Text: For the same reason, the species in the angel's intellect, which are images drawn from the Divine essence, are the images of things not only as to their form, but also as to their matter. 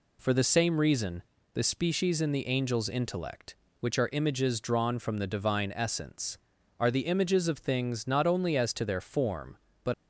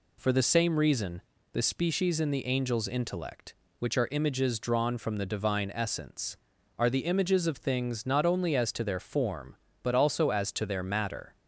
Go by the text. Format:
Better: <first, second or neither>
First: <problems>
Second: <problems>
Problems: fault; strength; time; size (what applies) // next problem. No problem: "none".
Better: second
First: stops before "also as to their matter"; at 9.9 s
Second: none